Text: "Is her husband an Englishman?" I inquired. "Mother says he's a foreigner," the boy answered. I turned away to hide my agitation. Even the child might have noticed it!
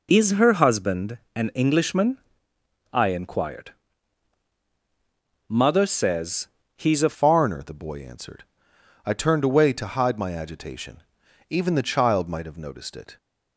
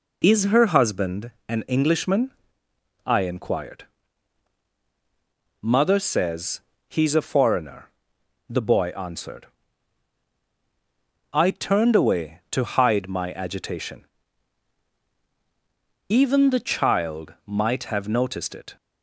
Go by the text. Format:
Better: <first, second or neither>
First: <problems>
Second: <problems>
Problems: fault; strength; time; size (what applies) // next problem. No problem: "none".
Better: second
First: pauses between "husband" and "an"; slight; at 1.1 s; 0.16 s long // pauses between "says" and "he's"; slight; at 6.4 s; 0.28 s long // changes voice at "foreigner"; from 7.1 s on; 6.0 s long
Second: pauses between "husband" and "an"; slight; at 1.3 s; 0.16 s long // pauses between "says" and "he's"; slight; at 6.6 s; 0.27 s long